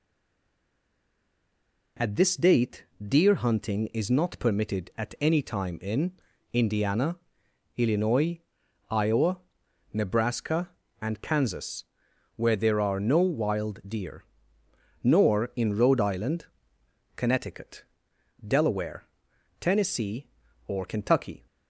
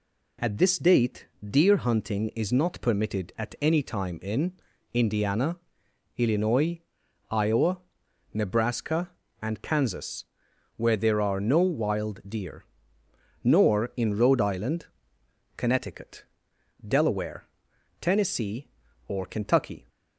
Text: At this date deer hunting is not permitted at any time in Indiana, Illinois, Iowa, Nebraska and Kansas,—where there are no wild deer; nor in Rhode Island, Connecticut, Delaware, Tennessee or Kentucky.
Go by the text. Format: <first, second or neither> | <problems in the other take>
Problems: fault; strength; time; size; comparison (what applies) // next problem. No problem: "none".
second | stays silent before the first word; noticeable; until 1.9 s; 1.9 s long // pauses between "date" and "deer"; slight; at 2.8 s; 0.18 s long; slight in the second // pauses between "in" and "Indiana"; at 6.1 s; 0.42 s long; also in the second